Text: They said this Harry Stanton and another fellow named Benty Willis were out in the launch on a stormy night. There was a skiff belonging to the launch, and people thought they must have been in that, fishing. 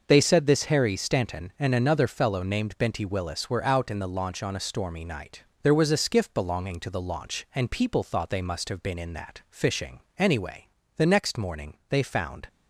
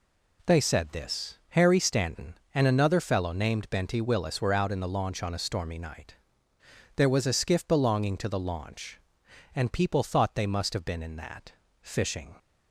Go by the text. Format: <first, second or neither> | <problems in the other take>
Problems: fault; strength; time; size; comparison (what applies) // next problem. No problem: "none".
second | starts louder than the rest; noticeable; until 1.0 s; 6 dB // goes on to say "Anyway the next morning they found"; strong; from 10.1 s on; 2.3 s long